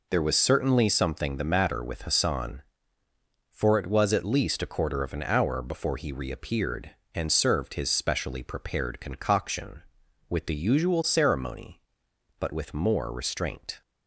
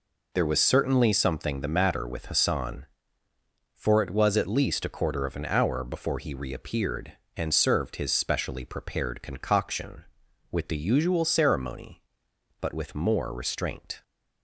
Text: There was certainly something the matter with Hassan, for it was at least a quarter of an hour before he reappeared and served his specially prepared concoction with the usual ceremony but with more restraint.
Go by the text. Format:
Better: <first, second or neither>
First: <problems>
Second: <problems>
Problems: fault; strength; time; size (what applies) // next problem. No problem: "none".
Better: neither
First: none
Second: none